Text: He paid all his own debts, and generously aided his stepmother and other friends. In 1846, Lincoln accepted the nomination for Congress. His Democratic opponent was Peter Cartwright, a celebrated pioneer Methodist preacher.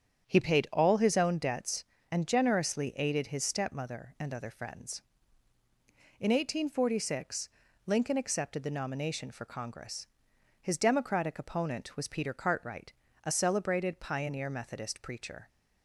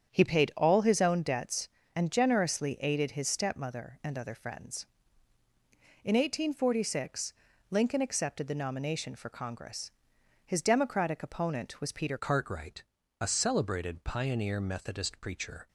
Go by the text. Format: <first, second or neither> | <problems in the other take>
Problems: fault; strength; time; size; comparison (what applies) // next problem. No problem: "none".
first | starts louder than the rest; strong; until 1.1 s; 8.5 dB; strong in the first // changes voice at "Cartwright"; from 12.1 s on; 3.5 s long